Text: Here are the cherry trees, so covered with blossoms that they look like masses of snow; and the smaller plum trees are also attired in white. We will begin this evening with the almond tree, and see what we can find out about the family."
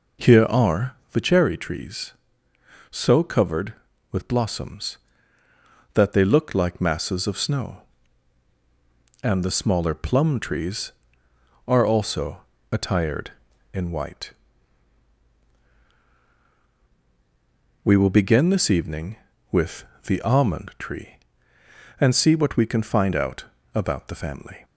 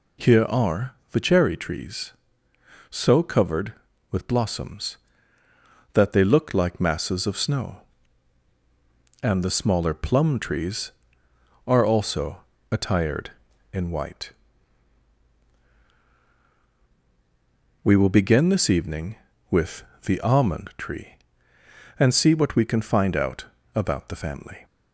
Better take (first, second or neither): second